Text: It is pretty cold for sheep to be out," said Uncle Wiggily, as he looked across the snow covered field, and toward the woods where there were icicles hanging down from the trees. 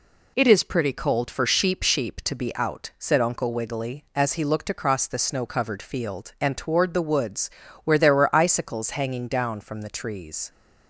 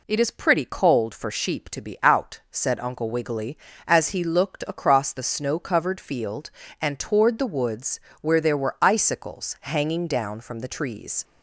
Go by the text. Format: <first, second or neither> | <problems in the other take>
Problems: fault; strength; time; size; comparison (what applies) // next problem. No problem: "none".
second | says "sheep" twice; at 1.8 s // pauses between "woods" and "where"; slight; at 7.4 s; 0.34 s long; slight in the second